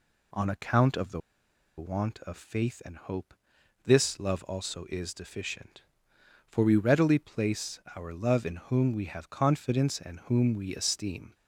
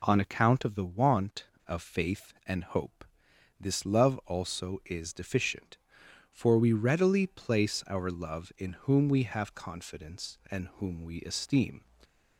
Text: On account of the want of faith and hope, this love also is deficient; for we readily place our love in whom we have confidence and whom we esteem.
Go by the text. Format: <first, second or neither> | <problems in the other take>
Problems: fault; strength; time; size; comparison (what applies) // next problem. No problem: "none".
second | pauses between "the" and "want"; noticeable; at 1.2 s; 0.57 s long // pauses between "place" and "our"; slight; at 7.7 s; 0.16 s long